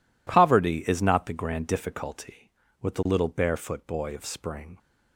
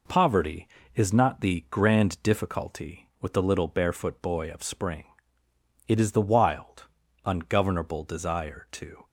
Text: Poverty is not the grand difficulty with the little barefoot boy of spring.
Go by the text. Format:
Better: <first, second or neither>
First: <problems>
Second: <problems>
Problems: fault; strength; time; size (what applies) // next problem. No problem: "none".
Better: first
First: none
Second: goes on to say "It is the wild ungovernable desire to"; strong; from 5.8 s on; 3.1 s long